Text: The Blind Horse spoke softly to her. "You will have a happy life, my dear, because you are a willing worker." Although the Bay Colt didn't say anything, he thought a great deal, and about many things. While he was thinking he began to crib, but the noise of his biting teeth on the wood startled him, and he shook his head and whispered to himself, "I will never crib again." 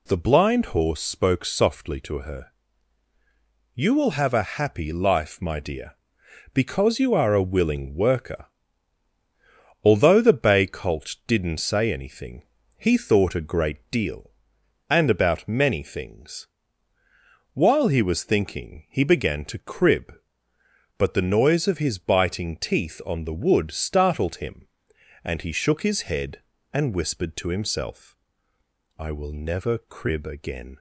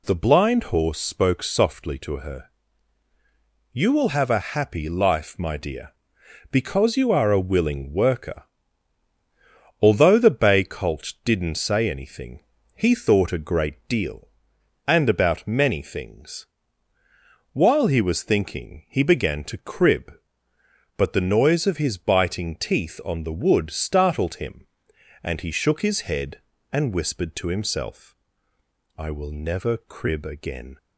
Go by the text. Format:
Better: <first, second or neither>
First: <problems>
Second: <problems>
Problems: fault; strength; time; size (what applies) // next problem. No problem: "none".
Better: neither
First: none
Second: none